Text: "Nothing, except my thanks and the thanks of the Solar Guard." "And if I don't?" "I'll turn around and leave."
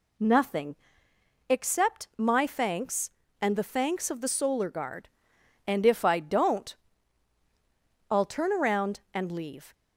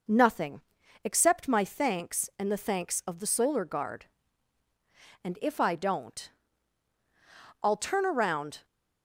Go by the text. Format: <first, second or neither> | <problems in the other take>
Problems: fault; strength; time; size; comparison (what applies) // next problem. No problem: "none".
first | stops before "and leave"; at 8.6 s